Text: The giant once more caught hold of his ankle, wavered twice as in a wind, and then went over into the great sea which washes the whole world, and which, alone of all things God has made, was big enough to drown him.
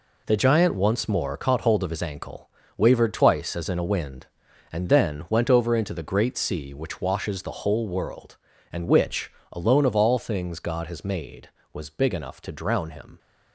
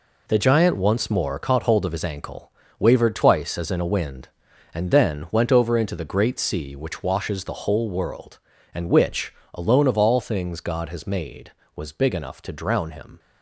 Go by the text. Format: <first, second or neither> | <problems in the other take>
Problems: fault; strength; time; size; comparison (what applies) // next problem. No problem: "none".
neither | none